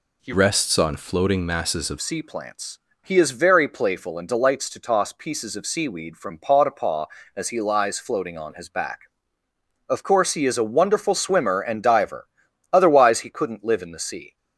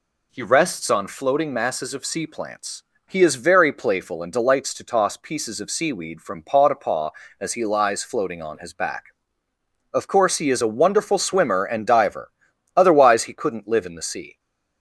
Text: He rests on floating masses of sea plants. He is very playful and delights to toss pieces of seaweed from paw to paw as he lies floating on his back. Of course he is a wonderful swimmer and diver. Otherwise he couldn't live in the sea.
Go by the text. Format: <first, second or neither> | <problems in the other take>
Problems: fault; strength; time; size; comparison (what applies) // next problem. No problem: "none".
second | changes voice from "rests" to "of"; from 0.3 to 1.9 s; 1.6 s long